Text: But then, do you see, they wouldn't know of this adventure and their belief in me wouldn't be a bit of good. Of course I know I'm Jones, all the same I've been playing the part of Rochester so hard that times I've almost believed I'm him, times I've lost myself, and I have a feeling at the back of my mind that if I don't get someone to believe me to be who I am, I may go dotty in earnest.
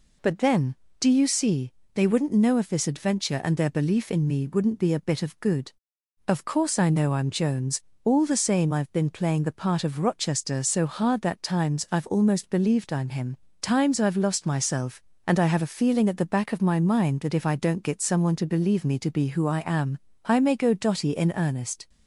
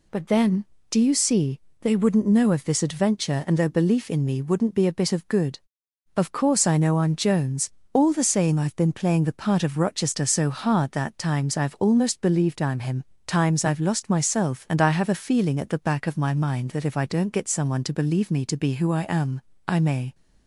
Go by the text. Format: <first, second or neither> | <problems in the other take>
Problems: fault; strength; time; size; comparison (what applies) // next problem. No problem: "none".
first | stops before "go dotty in earnest"; at 20.1 s